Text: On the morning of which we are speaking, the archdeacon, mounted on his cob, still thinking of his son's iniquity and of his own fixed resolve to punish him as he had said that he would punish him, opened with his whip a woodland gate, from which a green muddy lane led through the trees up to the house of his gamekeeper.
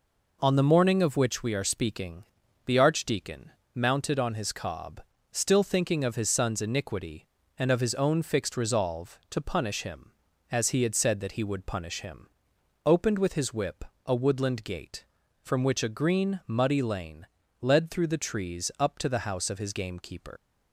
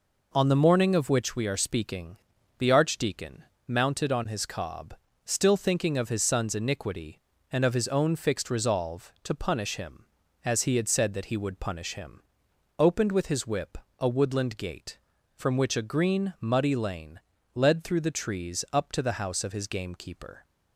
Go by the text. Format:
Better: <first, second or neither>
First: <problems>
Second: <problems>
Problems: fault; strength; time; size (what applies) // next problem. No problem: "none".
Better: second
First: pauses between "whip" and "a"; slight; at 13.8 s; 0.24 s long // pauses between "lane" and "led"; slight; at 17.2 s; 0.34 s long // leaves "gamekeeper" unfinished; at 20.3 s; 115 ms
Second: pauses between "whip" and "a"; slight; at 13.7 s; 0.24 s long // pauses between "lane" and "led"; slight; at 17.1 s; 0.34 s long